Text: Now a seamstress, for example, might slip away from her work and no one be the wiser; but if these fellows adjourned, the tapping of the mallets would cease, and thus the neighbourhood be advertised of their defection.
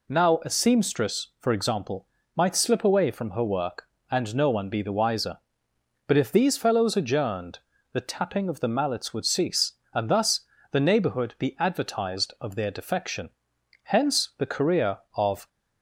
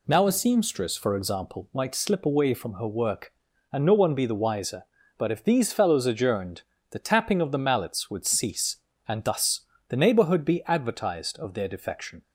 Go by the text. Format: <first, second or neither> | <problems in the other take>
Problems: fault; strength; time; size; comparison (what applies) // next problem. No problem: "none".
second | pauses between "thus" and "the"; slight; at 10.4 s; 0.28 s long; slight in the second // goes on to say "Hence the career of"; from 13.8 s on; 1.5 s long